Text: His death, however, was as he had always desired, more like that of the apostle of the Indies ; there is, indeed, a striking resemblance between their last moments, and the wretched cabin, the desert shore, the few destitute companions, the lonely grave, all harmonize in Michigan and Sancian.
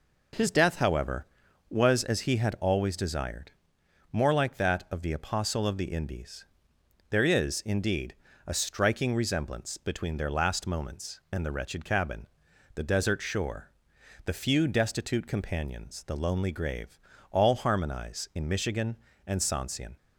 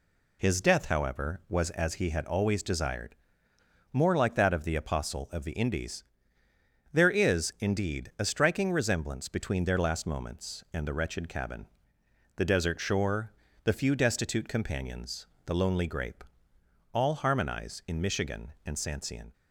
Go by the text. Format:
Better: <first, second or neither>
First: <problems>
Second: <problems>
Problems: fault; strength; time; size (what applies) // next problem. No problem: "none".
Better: first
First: none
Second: says "grape" for "grave"; at 15.8 s